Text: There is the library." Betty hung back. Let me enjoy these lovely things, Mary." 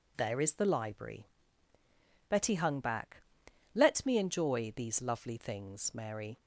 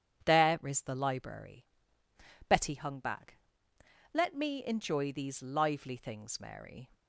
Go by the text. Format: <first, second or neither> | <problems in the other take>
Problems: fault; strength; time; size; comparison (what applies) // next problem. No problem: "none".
first | says "lively" for "lovely"; at 5.4 s